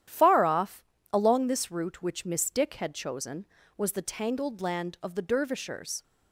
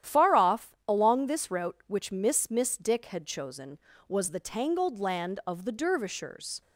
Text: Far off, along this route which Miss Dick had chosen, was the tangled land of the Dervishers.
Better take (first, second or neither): first